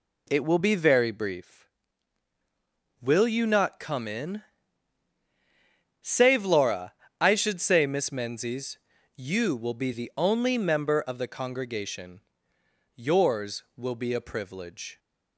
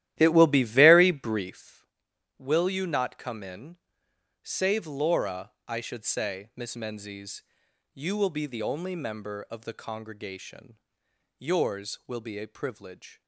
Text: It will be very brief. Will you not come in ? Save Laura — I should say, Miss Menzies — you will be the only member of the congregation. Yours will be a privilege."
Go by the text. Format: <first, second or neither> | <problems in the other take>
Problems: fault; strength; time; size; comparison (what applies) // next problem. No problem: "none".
first | starts louder than the rest; strong; until 1.6 s; 13 dB